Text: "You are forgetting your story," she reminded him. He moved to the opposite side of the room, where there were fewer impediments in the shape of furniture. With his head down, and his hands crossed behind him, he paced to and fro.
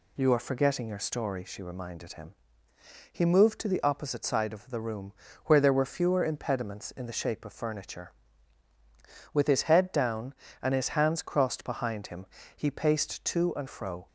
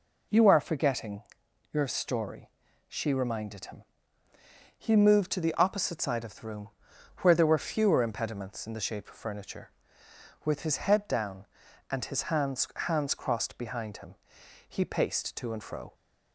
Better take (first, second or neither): first